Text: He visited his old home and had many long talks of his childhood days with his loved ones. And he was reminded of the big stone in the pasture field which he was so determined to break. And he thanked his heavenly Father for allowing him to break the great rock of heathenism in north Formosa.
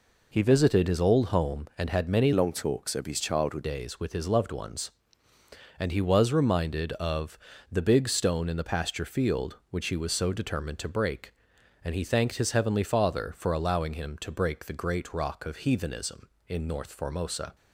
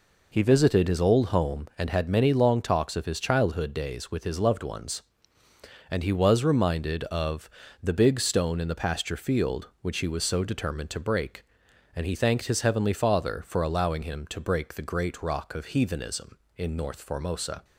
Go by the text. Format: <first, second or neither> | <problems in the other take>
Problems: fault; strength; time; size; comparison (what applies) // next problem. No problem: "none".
second | changes voice from "long" to "childhood"; from 2.3 to 3.6 s; 1.3 s long // pauses between "of" and "the"; slight; at 7.3 s; 0.32 s long; slight in the second